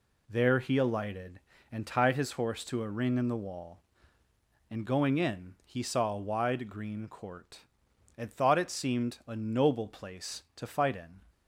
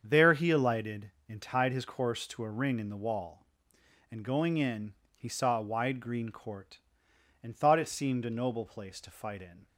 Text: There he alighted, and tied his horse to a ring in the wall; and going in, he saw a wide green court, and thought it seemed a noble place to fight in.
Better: first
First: none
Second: starts louder than the rest; strong; until 1.0 s; 7.5 dB // says "course" for "horse"; at 1.8 s

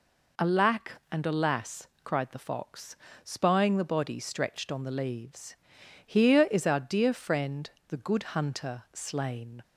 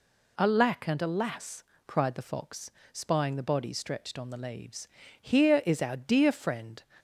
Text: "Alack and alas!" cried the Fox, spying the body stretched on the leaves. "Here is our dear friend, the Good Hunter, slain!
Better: first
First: none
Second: stops before "the Good Hunter slain"; at 6.9 s

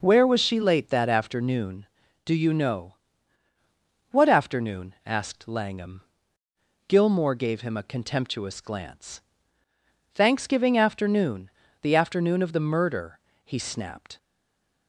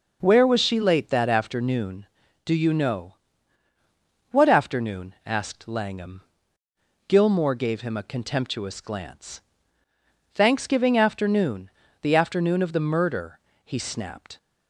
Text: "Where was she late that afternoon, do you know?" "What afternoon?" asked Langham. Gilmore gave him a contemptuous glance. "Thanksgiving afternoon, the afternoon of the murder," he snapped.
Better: second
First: stays silent after the last word; slight; from 14.1 s on; 0.7 s long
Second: none

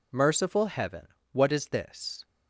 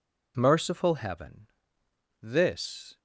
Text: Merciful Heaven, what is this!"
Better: first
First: none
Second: skips "what is"; at 1.8 s

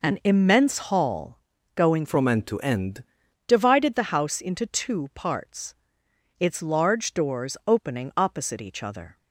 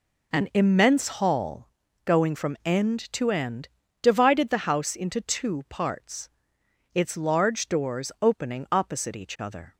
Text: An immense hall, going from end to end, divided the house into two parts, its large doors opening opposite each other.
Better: second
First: changes voice from "from" to "end"; from 2.0 to 3.0 s; 1.0 s long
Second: none

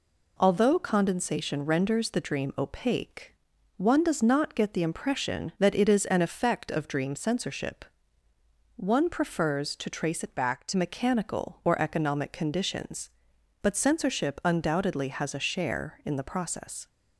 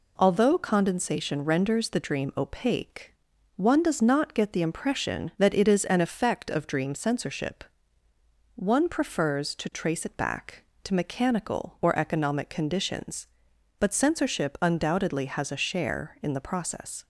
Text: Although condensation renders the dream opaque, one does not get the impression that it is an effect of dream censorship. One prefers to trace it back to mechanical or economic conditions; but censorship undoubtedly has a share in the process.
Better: second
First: changes voice from "back" to "to"; from 10.3 to 10.7 s; 0.4 s long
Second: none

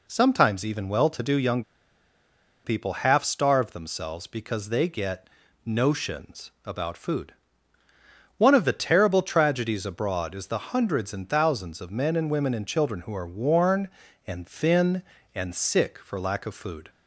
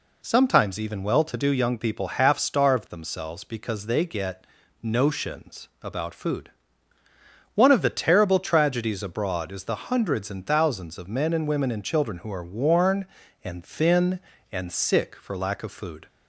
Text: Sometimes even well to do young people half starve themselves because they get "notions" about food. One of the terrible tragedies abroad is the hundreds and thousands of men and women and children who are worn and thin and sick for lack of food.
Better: second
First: pauses between "young" and "people"; at 1.6 s; 1.0 s long // pauses between "get" and "notions"; slight; at 5.2 s; 0.34 s long // pauses between "notions" and "about"; slight; at 6.4 s; 0.16 s long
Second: pauses between "get" and "notions"; slight; at 4.4 s; 0.34 s long // pauses between "notions" and "about"; slight; at 5.6 s; 0.16 s long

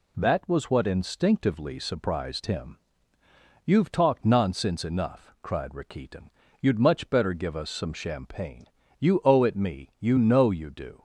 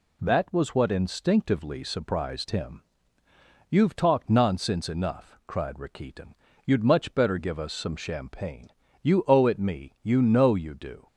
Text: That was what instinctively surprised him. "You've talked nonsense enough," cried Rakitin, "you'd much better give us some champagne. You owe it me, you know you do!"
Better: neither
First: none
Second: none

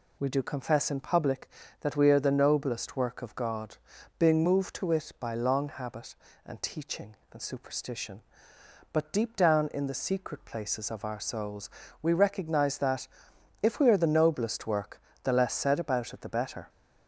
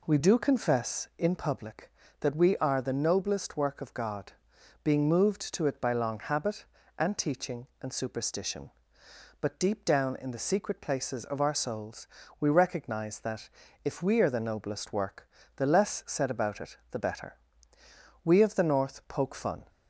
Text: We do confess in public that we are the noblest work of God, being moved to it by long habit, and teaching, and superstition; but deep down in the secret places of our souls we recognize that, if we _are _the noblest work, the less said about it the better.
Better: first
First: pauses between "souls" and "we"; slight; at 11.7 s; 0.32 s long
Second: pauses between "souls" and "we"; slight; at 12.0 s; 0.32 s long // pauses between "it" and "the"; slight; at 16.7 s; 0.16 s long // goes on to say "We of the North poke fun"; from 18.2 s on; 1.4 s long

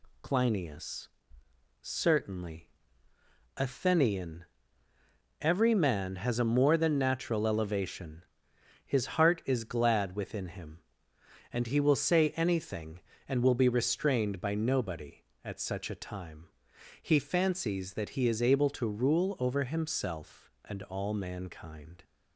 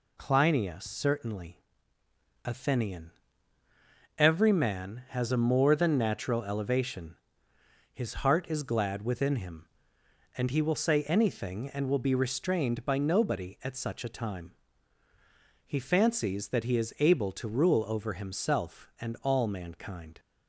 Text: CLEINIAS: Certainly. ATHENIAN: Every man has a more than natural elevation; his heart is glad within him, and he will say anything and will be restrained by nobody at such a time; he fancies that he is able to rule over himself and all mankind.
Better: neither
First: none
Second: none

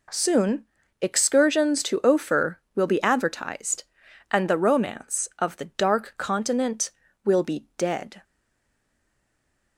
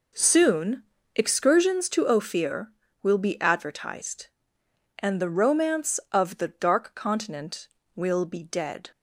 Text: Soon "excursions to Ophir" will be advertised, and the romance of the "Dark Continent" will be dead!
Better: second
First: pauses between "Soon" and "excursions"; at 0.6 s; 0.38 s long // stays silent after the last word; noticeable; from 8.2 s on; 1.5 s long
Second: pauses between "Soon" and "excursions"; slight; at 0.8 s; 0.32 s long

